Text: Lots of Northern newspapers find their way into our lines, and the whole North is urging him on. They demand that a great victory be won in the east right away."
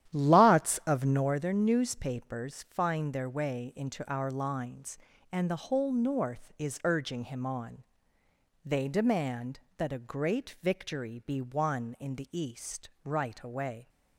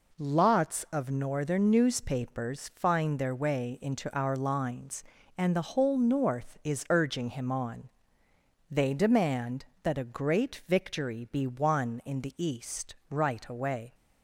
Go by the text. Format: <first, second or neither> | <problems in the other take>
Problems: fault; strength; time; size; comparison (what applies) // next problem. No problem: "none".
second | starts louder than the rest; strong; until 1.4 s; 11.5 dB // pauses between "east" and "right"; slight; at 12.8 s; 0.16 s long; slight in the second